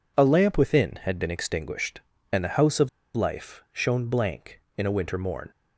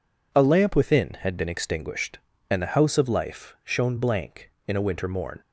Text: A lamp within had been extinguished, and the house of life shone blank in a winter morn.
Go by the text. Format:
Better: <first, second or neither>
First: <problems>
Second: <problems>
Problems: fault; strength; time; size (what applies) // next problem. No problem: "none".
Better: second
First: pauses between "of" and "life"; slight; at 2.8 s; 0.26 s long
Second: none